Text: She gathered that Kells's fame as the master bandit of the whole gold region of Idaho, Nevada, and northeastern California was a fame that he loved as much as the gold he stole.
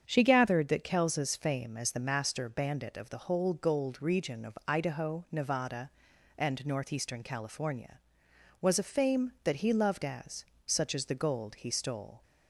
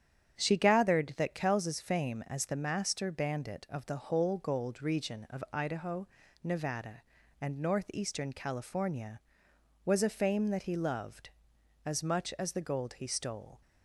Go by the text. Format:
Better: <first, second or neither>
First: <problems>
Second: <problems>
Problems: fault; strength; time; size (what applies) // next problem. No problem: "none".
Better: second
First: starts louder than the rest; strong; until 1.0 s; 7.5 dB // says "such" for "much"; at 10.6 s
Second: starts louder than the rest; strong; until 1.4 s; 8.5 dB